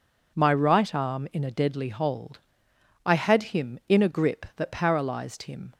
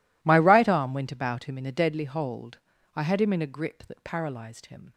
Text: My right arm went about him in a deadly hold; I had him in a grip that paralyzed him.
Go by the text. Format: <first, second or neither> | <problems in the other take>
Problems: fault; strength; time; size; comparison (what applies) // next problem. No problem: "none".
second | skips "went about him"; at 1.2 s